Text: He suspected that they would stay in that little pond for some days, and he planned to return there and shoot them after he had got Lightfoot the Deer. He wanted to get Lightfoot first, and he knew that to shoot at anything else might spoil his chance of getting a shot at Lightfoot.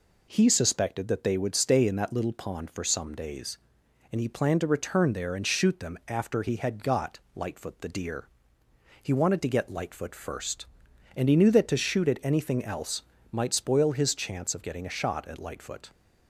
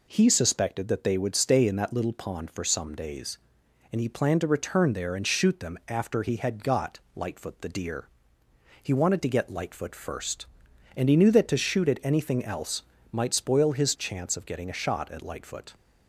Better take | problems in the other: neither | pauses between "got" and "Lightfoot"; slight; the same in both // pauses between "else" and "might"; slight; the same in both

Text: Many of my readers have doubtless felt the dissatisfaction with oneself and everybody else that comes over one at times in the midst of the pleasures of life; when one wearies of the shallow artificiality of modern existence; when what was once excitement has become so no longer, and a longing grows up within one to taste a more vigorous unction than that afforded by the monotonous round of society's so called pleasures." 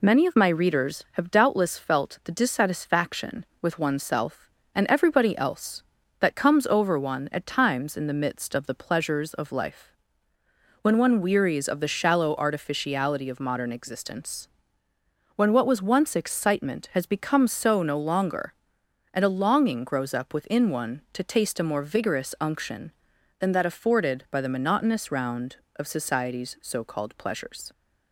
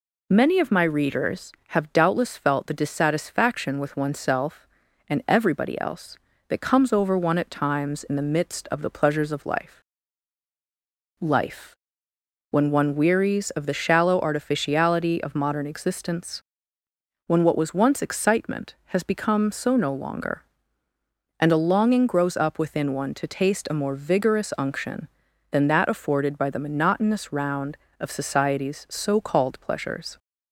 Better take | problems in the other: first | says "life" twice; at 11.2 s

